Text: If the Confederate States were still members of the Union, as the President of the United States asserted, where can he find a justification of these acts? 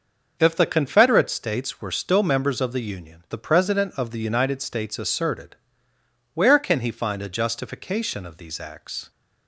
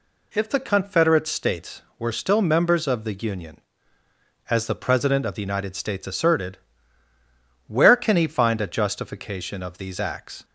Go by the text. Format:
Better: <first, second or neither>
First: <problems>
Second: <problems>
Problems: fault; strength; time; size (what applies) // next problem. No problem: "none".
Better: second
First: skips "as"; at 3.2 s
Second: none